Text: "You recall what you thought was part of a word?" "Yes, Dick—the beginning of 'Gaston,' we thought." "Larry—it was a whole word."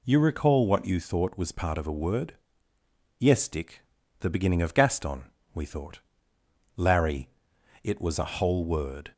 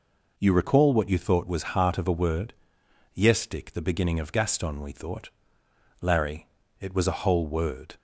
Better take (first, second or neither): first